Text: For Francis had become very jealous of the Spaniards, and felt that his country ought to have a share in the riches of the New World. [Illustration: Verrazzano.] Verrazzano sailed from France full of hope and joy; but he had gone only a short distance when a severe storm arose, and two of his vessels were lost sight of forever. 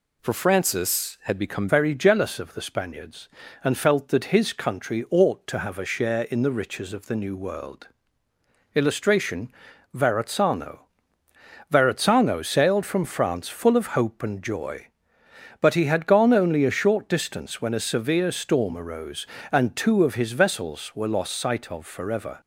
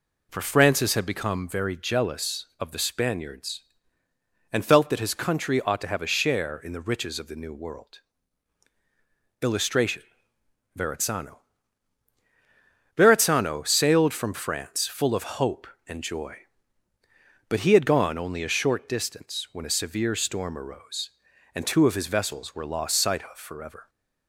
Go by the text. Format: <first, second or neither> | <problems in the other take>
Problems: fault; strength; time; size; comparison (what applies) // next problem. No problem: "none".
second | changes voice at "very"; from 1.6 s on; 20.8 s long